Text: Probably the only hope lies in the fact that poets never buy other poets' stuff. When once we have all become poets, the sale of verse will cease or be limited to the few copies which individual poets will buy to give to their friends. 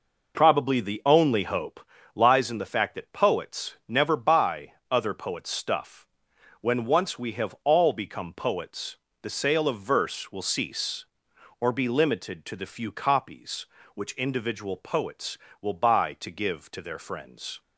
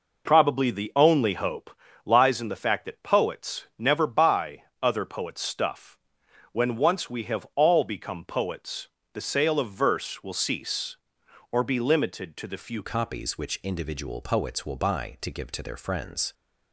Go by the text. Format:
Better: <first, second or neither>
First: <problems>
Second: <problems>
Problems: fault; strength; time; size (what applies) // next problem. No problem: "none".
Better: first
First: pauses between "hope" and "lies"; slight; at 1.7 s; 0.34 s long // pauses between "buy" and "other"; slight; at 4.7 s; 0.17 s long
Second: pauses between "hope" and "lies"; slight; at 1.7 s; 0.34 s long // pauses between "buy" and "other"; slight; at 4.6 s; 0.18 s long // changes voice at "copies"; from 12.8 s on; 3.5 s long